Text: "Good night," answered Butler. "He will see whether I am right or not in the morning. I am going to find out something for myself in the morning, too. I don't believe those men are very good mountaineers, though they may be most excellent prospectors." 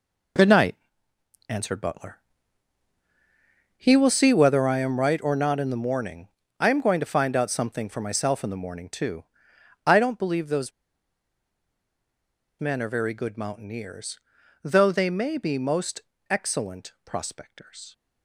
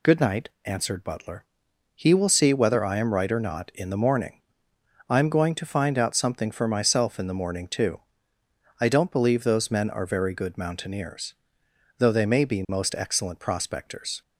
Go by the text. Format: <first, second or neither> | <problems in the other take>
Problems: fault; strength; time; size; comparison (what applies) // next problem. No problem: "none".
second | pauses between "those" and "men"; strong; at 10.7 s; 1.8 s long // pauses between "most" and "excellent"; slight; at 16.0 s; 0.30 s long